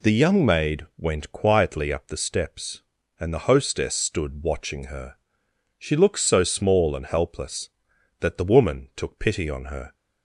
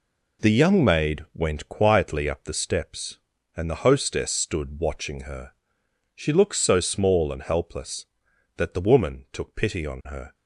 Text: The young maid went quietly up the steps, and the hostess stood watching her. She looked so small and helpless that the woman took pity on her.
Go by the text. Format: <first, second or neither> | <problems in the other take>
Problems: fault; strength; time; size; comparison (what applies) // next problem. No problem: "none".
first | gets quieter; strong; throughout; 8 dB